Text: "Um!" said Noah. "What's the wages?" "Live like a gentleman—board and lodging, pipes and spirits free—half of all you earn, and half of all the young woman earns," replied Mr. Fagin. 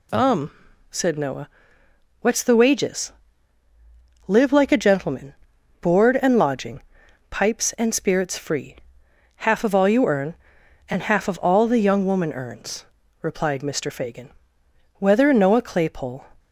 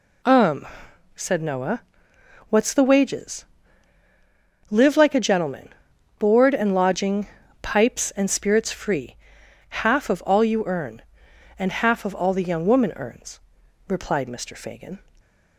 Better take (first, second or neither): second